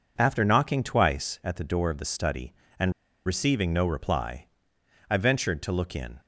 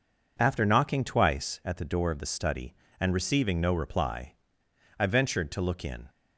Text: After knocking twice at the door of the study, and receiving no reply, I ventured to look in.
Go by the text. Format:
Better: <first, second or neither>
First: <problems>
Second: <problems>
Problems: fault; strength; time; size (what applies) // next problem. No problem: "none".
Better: second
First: pauses between "and" and "receiving"; slight; at 2.9 s; 0.34 s long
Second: none